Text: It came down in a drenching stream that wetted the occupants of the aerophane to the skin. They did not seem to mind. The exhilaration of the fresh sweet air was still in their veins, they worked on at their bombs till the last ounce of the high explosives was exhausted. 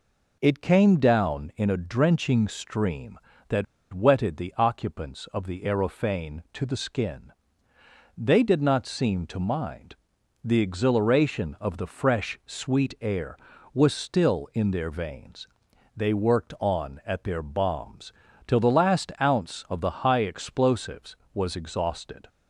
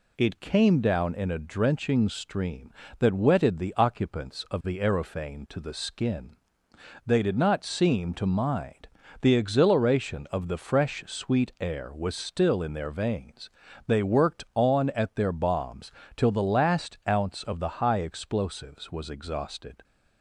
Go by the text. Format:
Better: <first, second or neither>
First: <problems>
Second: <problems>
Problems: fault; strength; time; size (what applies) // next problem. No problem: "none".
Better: second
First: pauses between "that" and "wetted"; slight; at 3.6 s; 0.28 s long // pauses between "bombs" and "till"; slight; at 18.1 s; 0.32 s long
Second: pauses between "bombs" and "till"; slight; at 15.9 s; 0.24 s long